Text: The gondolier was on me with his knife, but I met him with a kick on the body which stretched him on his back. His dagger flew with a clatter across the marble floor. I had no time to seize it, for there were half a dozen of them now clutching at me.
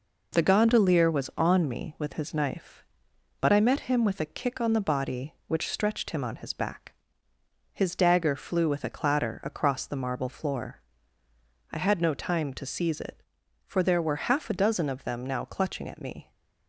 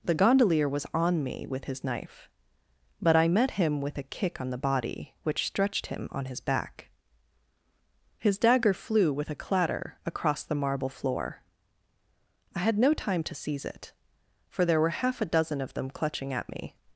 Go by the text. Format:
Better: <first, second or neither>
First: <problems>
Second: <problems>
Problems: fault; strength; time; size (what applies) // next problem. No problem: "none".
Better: first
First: none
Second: skips "now"; at 15.8 s